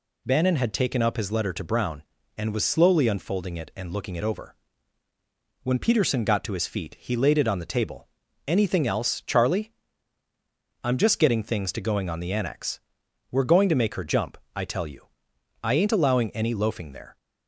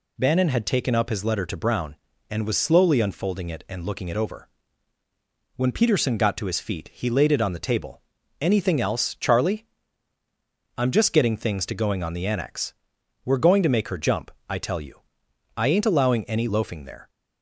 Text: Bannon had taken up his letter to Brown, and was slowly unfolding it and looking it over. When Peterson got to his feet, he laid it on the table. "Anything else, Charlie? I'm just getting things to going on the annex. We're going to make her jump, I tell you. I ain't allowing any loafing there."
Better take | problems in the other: neither | none

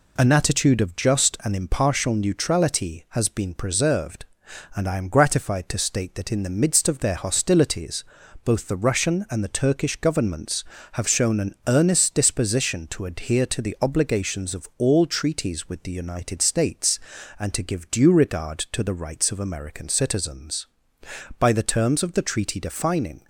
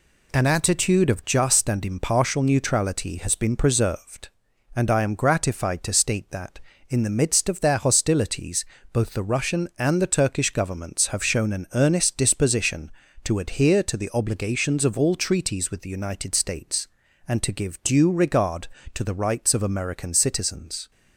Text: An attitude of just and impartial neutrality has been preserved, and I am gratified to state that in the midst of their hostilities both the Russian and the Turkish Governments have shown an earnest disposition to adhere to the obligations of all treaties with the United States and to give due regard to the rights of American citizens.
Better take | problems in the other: second | pauses between "hostilities" and "both"; at 8.0 s; 0.40 s long; slight in the second // goes on to say "By the terms of the treaty defining"; strong; from 21.3 s on; 1.8 s long

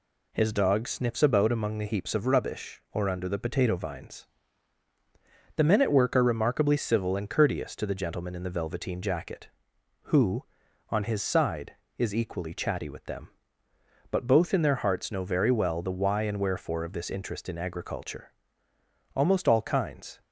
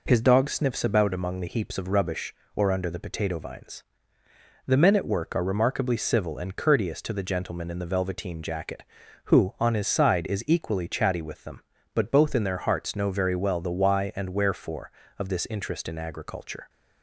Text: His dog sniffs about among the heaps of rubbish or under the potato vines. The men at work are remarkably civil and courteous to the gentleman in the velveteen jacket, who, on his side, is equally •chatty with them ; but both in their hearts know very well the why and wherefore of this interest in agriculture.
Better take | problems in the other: second | goes on to say "Almost all kinds"; noticeable; from 19.1 s on; 1.0 s long

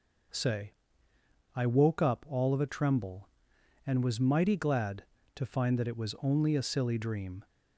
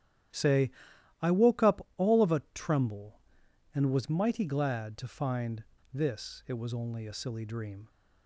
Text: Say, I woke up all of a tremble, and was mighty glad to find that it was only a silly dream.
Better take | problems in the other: first | starts louder than the rest; strong; until 1.8 s; 11.5 dB // says "this" for "that"; at 5.9 s

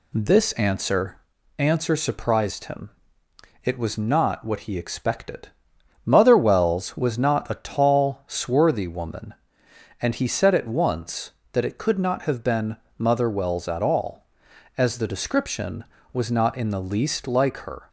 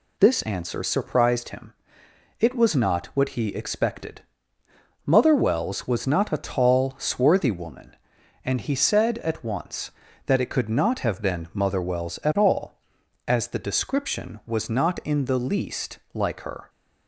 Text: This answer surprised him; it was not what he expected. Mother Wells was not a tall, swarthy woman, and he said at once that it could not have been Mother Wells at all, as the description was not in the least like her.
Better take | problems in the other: second | says "answer" twice; at 1.5 s // pauses between "been" and "Mother"; slight; at 12.7 s; 0.24 s long

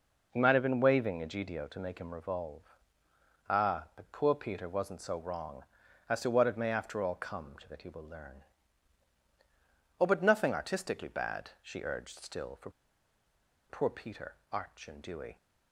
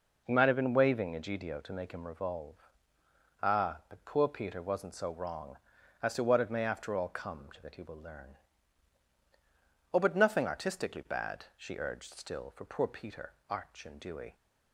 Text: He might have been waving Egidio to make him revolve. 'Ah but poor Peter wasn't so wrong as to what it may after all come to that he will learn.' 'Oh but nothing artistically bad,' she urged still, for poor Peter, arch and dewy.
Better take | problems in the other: second | pauses between "for" and "poor"; at 12.6 s; 0.99 s long

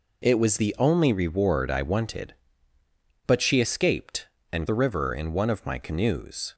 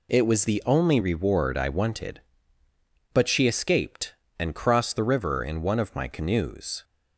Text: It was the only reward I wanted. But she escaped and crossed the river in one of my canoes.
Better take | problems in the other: second | skips "crossed"; at 4.6 s

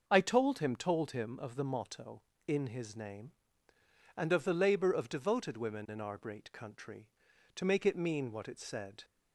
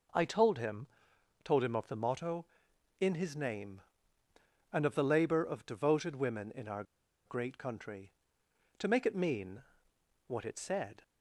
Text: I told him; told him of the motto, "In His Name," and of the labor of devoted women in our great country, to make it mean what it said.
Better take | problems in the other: first | pauses between "our" and "great"; at 6.8 s; 0.42 s long // pauses between "mean" and "what"; noticeable; at 9.6 s; 0.64 s long

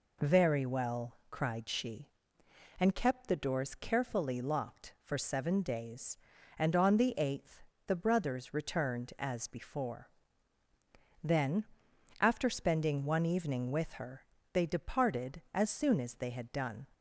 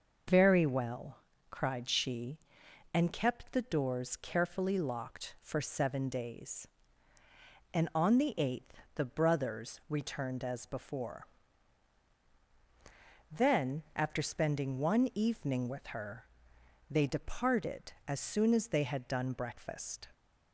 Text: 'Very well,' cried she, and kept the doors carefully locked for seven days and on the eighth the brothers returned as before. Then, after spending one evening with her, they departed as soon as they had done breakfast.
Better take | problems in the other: second | pauses between "eighth" and "the"; slight; at 7.6 s; 0.24 s long; slight in the second // stops before "breakfast"; at 16.9 s

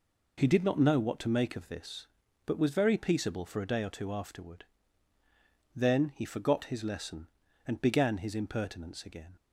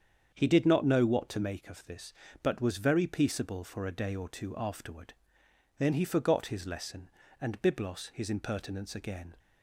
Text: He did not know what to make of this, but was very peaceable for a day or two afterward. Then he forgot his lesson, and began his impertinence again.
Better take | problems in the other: first | starts louder than the rest; strong; until 1.3 s; 7.5 dB // says "byblos" for "began"; at 7.6 s

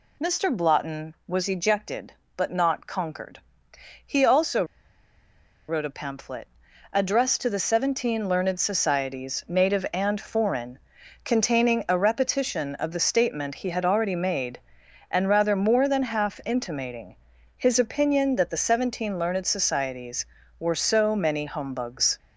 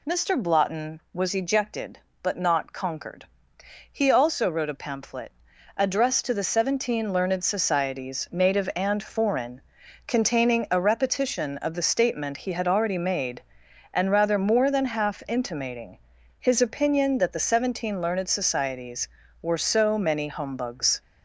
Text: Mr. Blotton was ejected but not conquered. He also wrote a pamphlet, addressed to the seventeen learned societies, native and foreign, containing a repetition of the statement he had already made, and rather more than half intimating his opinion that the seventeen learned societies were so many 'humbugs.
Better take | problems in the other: second | pauses between "also" and "wrote"; at 4.6 s; 1.0 s long // pauses between "intimating" and "his"; at 17.1 s; 0.40 s long; also in the second

